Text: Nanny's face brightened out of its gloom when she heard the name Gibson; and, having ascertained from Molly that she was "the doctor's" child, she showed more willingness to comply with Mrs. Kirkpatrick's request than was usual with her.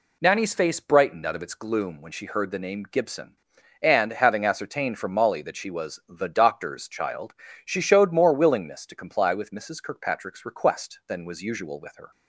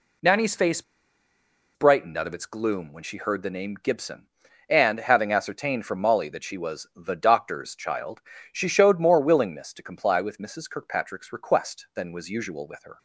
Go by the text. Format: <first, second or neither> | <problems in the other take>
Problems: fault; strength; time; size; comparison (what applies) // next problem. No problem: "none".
first | pauses between "face" and "brightened"; noticeable; at 0.8 s; 0.93 s long